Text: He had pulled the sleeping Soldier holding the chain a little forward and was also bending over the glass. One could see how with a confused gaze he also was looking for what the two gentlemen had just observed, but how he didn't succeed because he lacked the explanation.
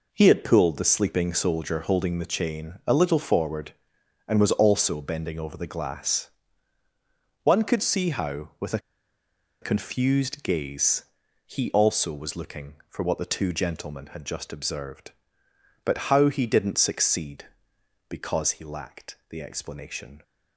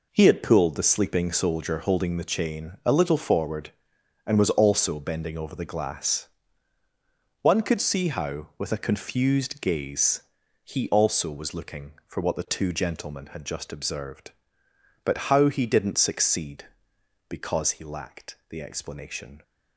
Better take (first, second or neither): second